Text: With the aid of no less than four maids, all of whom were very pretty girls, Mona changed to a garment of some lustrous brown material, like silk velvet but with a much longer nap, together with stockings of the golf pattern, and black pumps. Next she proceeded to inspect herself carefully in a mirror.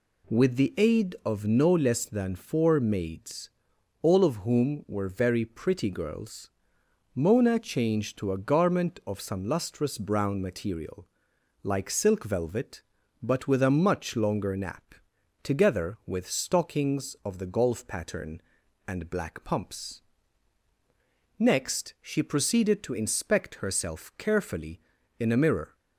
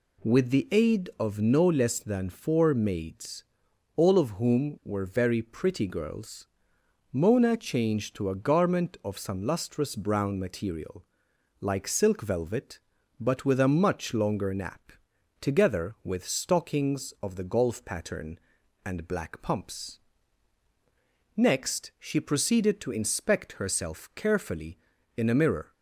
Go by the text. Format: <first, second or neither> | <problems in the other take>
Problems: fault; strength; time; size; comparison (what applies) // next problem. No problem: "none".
neither | none